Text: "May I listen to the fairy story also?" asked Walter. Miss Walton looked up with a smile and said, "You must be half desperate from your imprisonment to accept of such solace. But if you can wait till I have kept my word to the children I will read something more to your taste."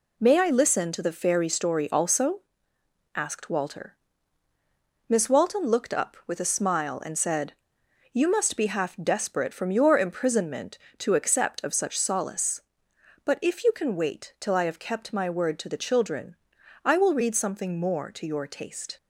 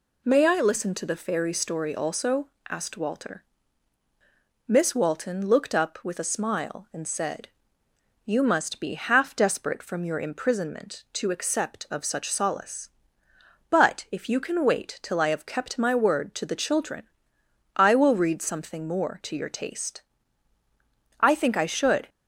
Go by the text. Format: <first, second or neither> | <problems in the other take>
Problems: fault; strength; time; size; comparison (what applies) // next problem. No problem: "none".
first | pauses between "children" and "I"; noticeable; at 17.0 s; 0.70 s long; noticeable in the first // goes on to say "I think I should"; noticeable; from 21.2 s on; 0.88 s long